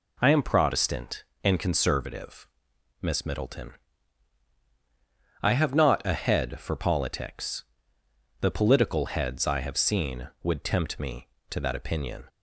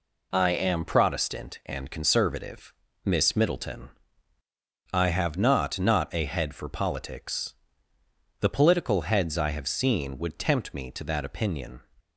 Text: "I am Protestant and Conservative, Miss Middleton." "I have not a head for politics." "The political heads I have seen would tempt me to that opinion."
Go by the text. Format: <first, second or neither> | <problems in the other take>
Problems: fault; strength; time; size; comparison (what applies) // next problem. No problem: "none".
first | says "not" twice; at 5.7 s